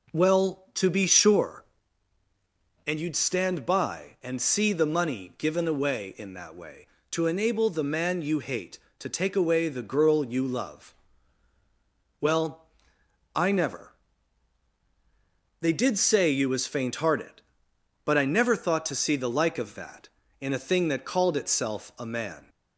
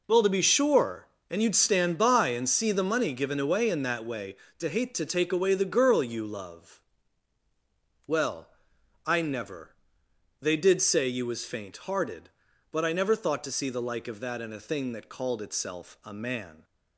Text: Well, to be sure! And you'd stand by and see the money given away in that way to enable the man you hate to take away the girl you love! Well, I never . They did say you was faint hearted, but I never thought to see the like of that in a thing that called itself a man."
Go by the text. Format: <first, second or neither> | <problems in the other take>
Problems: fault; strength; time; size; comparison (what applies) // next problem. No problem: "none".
first | skips "enable the man you"; at 4.6 s